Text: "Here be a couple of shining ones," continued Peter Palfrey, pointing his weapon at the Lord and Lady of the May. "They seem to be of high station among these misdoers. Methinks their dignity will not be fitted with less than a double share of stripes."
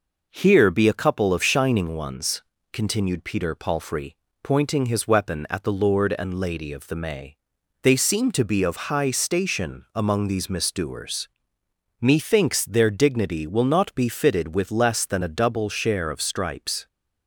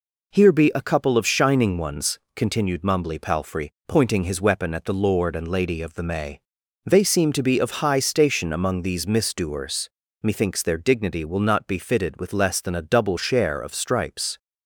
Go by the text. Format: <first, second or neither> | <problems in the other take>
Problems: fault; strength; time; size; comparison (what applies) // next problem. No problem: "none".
first | says "Mumbly" for "Peter"; at 2.8 s